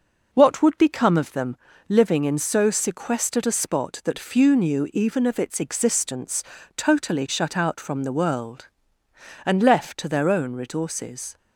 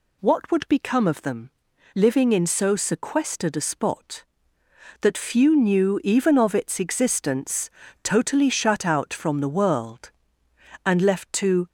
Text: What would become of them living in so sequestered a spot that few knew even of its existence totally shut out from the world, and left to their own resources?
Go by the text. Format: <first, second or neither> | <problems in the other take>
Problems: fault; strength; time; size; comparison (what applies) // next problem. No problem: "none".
first | pauses between "them" and "living"; at 1.5 s; 0.44 s long; slight in the first // pauses between "existence" and "totally"; slight; at 7.7 s; 0.32 s long; slight in the first // stops before "their own resources"; at 11.6 s